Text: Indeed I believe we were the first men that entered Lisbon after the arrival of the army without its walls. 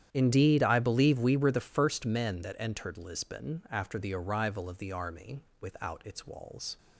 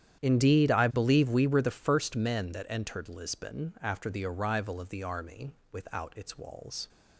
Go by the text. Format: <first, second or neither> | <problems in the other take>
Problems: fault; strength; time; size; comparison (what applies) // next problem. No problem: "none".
neither | starts louder than the rest; strong; the same in both // pauses between "army" and "without"; slight; the same in both